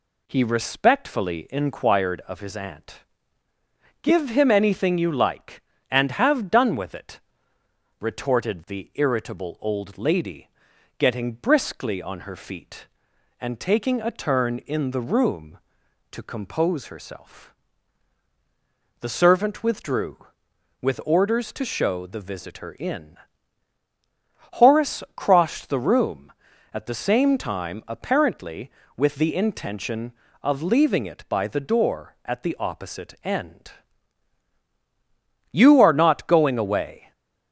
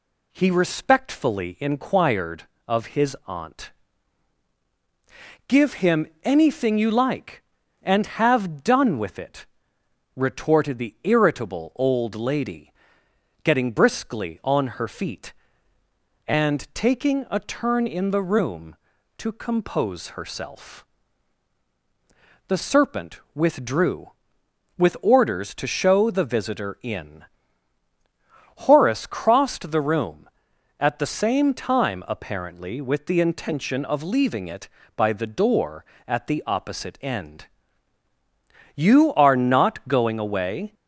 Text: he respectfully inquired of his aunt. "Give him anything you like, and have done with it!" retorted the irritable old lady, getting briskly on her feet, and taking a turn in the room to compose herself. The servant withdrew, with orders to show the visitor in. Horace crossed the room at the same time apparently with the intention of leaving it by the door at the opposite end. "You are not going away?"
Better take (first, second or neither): first